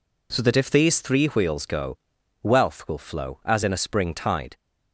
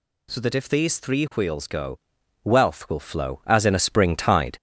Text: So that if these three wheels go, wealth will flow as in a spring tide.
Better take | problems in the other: first | gets louder; slight; throughout; 3 dB

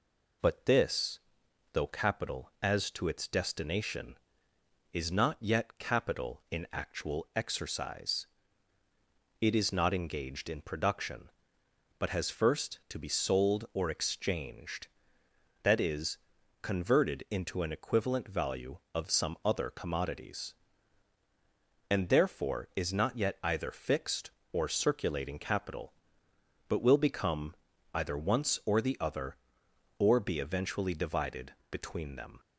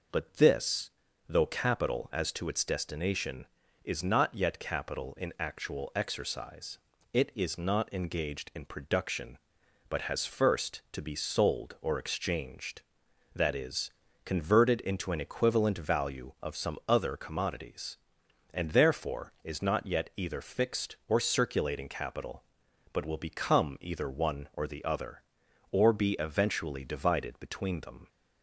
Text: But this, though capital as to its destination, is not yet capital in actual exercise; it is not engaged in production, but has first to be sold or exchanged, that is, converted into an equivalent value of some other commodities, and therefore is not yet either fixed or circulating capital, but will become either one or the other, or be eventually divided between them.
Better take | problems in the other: second | pauses between "become" and "either"; at 27.5 s; 0.40 s long // says "once" for "one"; at 28.1 s // pauses between "divided" and "between"; slight; at 31.5 s; 0.16 s long

